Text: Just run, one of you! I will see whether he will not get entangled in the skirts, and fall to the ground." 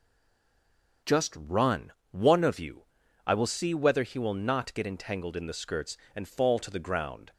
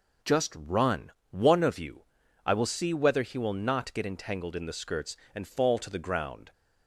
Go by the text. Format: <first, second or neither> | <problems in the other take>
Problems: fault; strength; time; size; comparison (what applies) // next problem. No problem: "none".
second | stays silent before the first word; until 1.0 s; 1.0 s long